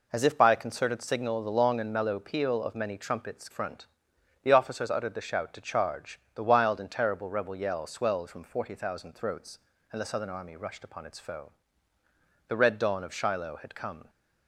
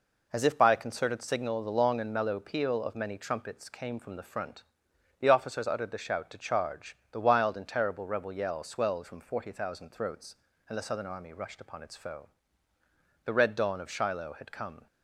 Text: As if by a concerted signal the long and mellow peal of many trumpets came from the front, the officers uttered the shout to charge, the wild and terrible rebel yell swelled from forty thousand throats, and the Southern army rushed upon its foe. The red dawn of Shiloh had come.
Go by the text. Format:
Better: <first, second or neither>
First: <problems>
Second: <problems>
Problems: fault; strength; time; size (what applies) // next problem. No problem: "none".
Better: second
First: skips "came from the"; at 3.5 s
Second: none